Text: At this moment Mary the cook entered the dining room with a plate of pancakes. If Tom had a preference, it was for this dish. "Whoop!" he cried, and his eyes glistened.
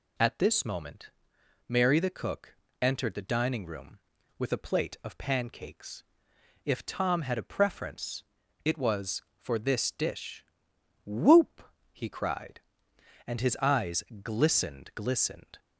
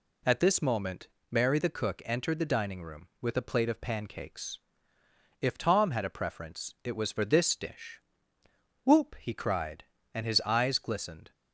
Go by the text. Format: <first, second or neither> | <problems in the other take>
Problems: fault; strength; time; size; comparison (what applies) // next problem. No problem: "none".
second | pauses between "moment" and "Mary"; noticeable; at 1.1 s; 0.56 s long; slight in the second // pauses between "cook" and "entered"; slight; at 2.5 s; 0.26 s long // pauses between "eyes" and "glistened"; slight; at 14.0 s; 0.18 s long // says "glistened" twice; at 14.9 s